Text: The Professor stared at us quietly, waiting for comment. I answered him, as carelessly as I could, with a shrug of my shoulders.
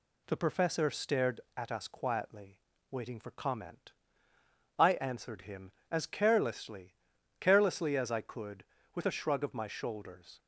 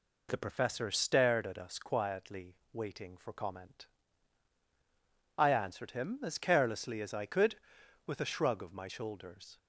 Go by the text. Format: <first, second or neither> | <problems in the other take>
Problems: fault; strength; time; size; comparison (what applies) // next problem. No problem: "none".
second | says "carelessly" twice; at 7.4 s